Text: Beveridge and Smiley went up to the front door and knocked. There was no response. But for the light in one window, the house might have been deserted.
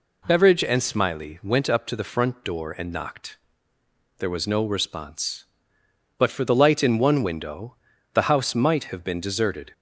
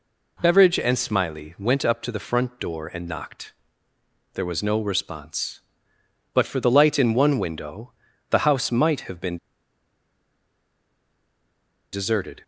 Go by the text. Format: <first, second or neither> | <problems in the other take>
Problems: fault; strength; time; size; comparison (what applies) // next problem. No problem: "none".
first | pauses between "been" and "deserted"; strong; at 9.3 s; 2.5 s long